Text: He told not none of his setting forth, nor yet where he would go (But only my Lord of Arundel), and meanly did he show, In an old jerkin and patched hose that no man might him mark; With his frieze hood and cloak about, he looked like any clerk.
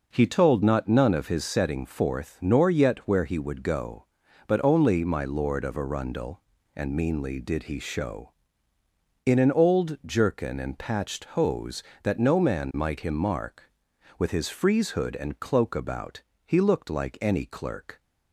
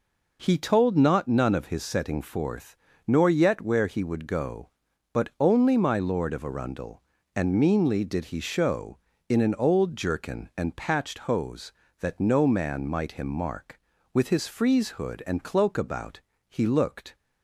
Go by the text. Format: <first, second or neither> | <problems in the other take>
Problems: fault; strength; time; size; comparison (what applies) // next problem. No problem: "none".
first | stops before "like any clerk"; at 17.1 s